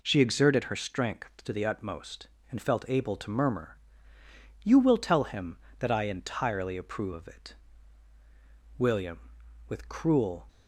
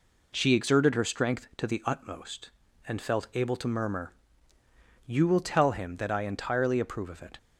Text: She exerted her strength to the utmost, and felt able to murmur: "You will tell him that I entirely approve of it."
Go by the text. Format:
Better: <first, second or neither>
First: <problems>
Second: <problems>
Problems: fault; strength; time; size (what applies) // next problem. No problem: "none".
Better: second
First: goes on to say "William with cruel"; strong; from 8.7 s on; 1.7 s long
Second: none